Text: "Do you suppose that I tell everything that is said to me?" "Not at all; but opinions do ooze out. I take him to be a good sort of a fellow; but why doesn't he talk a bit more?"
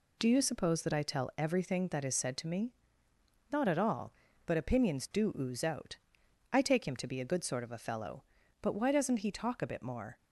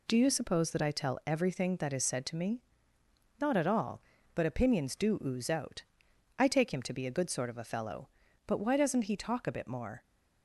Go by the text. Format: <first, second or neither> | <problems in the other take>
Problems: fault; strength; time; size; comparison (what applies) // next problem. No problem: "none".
neither | none